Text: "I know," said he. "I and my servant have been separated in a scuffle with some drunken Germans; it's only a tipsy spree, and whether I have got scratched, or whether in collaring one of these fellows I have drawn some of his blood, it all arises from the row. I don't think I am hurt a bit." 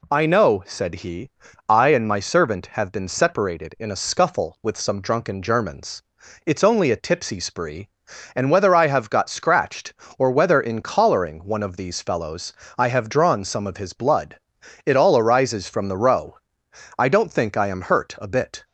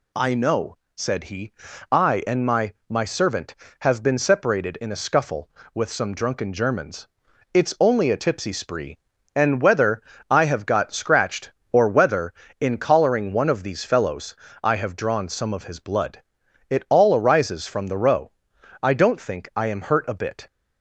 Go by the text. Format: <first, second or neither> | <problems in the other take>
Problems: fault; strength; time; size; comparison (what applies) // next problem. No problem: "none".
first | says "my" twice; at 2.9 s // pauses between "whether" and "I"; slight; at 10.0 s; 0.26 s long // pauses between "fellows" and "I"; slight; at 14.3 s; 0.26 s long; slight in the first